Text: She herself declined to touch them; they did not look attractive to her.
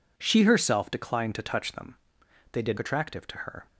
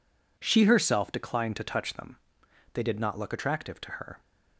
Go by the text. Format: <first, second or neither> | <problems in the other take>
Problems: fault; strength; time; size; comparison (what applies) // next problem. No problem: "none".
second | skips "not look"; at 2.7 s